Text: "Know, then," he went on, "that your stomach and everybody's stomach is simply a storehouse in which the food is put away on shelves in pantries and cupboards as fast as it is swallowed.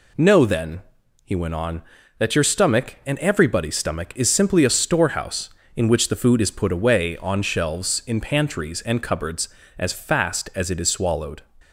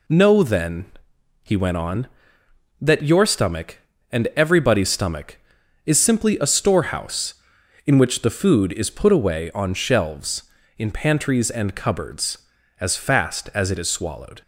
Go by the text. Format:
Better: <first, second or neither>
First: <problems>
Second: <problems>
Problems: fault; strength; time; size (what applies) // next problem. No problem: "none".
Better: neither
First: none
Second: none